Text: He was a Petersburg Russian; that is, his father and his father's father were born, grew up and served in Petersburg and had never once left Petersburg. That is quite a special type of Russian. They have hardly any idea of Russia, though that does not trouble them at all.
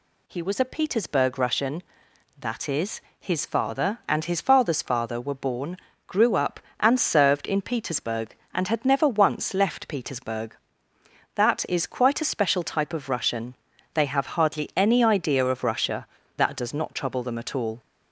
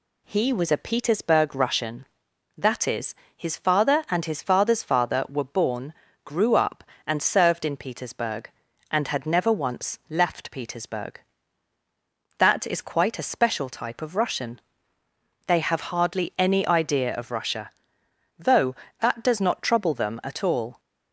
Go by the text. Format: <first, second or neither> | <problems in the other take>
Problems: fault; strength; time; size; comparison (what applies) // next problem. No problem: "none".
second | skips "though"; at 16.2 s